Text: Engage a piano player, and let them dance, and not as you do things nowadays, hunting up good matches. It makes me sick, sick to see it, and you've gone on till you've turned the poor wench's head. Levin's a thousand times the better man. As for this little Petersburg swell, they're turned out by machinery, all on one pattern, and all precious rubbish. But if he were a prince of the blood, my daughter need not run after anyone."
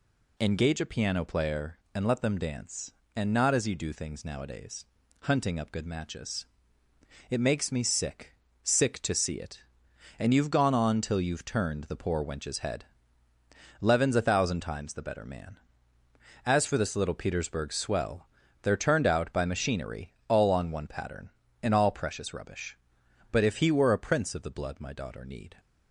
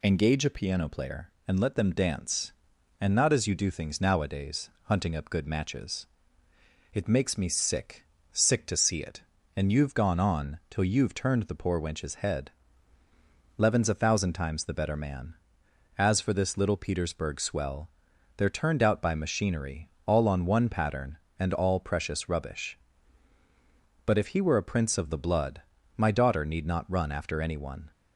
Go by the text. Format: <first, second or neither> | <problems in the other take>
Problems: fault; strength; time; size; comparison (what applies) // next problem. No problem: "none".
second | stops before "not run after anyone"; at 25.5 s